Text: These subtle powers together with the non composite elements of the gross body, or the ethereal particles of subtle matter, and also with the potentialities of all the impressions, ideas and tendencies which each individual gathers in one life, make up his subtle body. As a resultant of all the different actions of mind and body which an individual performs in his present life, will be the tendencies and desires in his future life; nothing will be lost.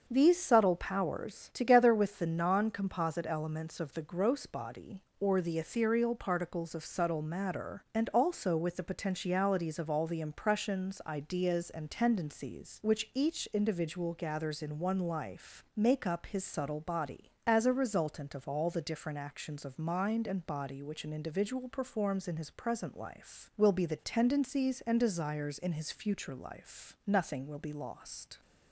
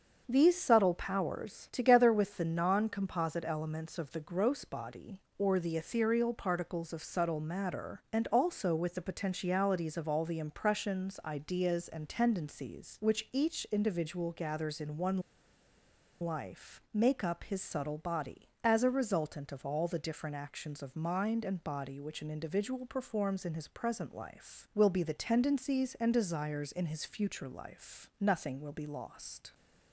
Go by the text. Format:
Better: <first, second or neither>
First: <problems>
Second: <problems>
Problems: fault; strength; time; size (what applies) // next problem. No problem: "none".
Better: first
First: starts louder than the rest; until 1.0 s; 6.5 dB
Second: starts louder than the rest; until 1.2 s; 6.5 dB // pauses between "one" and "life"; at 15.1 s; 1.0 s long